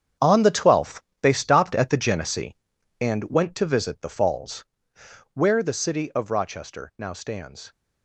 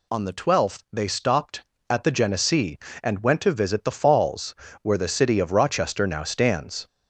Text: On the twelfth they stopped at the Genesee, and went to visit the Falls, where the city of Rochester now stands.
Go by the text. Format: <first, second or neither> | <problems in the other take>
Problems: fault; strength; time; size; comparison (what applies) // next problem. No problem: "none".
second | gets quieter; strong; throughout; 12 dB // pauses between "twelfth" and "they"; slight; at 1.0 s; 0.22 s long